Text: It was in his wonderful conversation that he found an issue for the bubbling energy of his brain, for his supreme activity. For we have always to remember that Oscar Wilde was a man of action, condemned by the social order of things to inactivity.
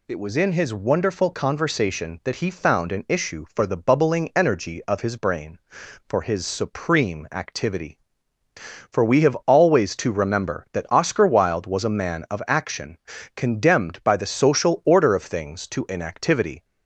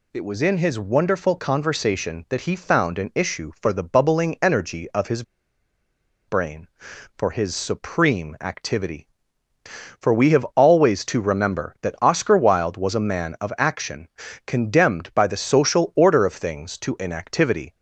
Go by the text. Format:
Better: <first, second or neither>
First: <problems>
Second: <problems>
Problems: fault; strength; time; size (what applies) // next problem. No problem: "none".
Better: first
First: none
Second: pauses between "his" and "brain"; at 5.2 s; 1.0 s long